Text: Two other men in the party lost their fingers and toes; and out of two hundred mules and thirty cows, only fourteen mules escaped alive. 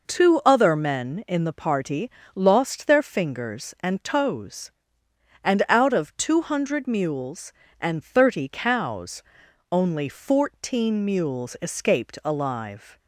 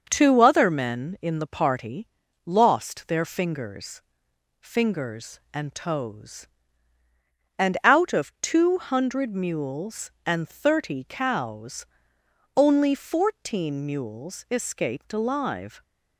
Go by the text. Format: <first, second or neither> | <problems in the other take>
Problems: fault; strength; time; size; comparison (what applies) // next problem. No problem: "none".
first | starts louder than the rest; noticeable; until 1.1 s; 6 dB // pauses between "party" and "lost"; slight; at 2.0 s; 0.36 s long; slight in the first // says "fingers" twice; at 4.5 s